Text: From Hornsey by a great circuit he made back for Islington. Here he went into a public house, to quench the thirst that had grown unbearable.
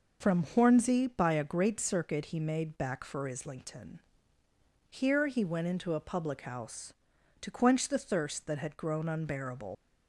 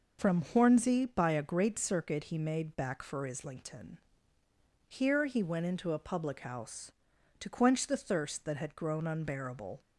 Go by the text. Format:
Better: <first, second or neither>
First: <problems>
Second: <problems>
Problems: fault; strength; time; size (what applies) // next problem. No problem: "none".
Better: second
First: leaves "unbearable" unfinished; at 9.7 s; 65 ms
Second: none